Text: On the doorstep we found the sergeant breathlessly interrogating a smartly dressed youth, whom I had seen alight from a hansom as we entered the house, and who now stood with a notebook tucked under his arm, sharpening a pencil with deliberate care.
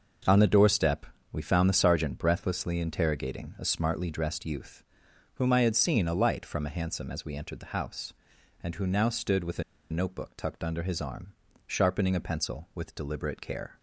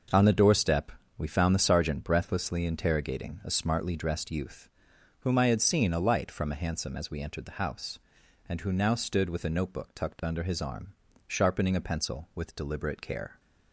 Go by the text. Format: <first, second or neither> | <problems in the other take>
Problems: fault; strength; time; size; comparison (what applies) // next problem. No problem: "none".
second | starts louder than the rest; noticeable; until 1.5 s; 6 dB; noticeable in the second // pauses between "doorstep" and "we"; slight; at 1.0 s; 0.28 s long; slight in the second // pauses between "a" and "notebook"; slight; at 9.6 s; 0.30 s long